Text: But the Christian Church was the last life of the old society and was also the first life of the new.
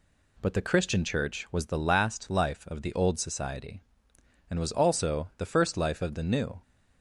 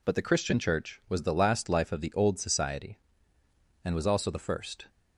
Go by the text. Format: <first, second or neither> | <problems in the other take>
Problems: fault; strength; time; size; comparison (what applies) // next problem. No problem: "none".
first | stops before "life of the new"; at 4.8 s